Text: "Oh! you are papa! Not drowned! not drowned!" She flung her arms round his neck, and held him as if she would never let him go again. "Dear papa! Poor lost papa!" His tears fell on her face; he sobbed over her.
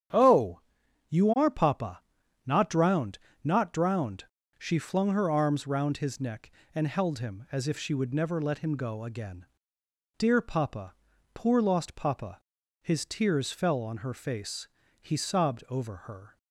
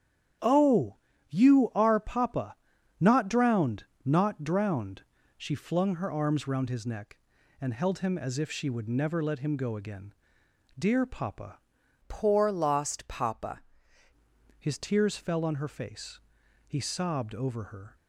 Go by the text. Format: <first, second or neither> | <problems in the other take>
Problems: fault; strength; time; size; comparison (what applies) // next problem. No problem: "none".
first | starts louder than the rest; strong; until 1.8 s; 10 dB; strong in the first // changes voice from "Poor" to "papa"; from 12.0 to 13.6 s; 1.6 s long